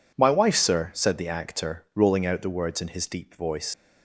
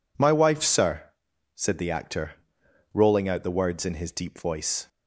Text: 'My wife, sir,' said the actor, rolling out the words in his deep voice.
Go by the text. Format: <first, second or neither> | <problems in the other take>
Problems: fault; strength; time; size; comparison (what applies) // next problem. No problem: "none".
second | leaves "voice" unfinished; at 3.7 s; 110 ms